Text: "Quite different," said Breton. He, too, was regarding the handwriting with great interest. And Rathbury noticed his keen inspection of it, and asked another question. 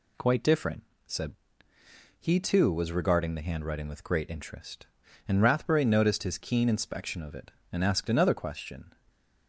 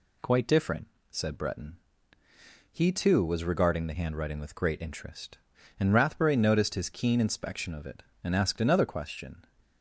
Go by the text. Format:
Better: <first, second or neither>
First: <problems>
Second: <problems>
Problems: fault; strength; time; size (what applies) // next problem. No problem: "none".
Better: second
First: skips "Breton"; at 1.7 s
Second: none